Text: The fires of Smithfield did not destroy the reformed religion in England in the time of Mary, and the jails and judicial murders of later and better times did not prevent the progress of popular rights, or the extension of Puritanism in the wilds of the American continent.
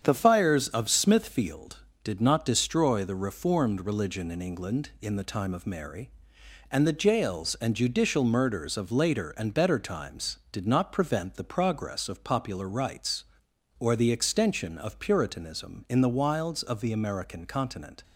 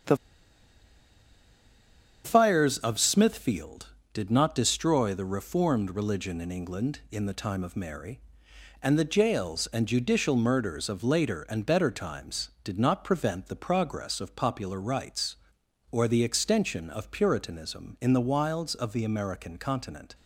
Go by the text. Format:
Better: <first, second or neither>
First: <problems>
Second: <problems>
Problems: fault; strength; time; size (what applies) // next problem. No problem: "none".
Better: first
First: starts louder than the rest; strong; until 1.0 s; 8 dB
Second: starts louder than the rest; strong; until 3.1 s; 8 dB // pauses between "The" and "fires"; strong; at 0.1 s; 2.0 s long